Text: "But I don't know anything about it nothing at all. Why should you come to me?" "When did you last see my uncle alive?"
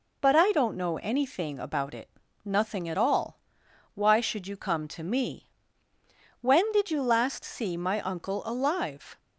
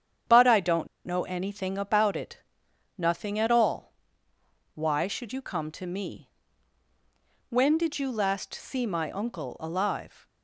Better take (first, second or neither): first